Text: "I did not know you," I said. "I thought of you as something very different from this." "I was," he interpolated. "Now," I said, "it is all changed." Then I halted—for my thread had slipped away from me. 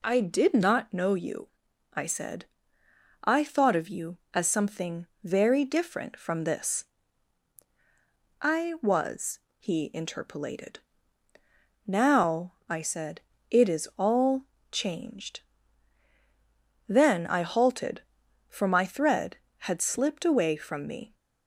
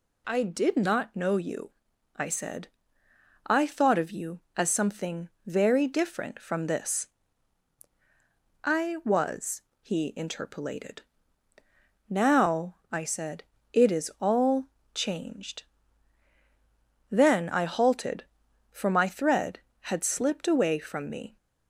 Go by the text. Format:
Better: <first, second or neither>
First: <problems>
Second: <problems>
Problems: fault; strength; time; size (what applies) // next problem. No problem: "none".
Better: second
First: starts louder than the rest; slight; until 1.1 s; 3 dB // pauses between "something" and "very"; slight; at 5.0 s; 0.18 s long // pauses between "all" and "changed"; slight; at 14.4 s; 0.26 s long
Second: pauses between "something" and "very"; slight; at 5.2 s; 0.18 s long // pauses between "all" and "changed"; slight; at 14.6 s; 0.26 s long